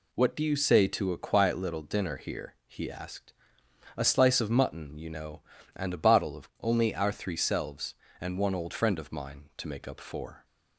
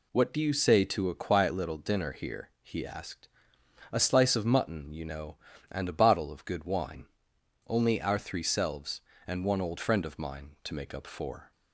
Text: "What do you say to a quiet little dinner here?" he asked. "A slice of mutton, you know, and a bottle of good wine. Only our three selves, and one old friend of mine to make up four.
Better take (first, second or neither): second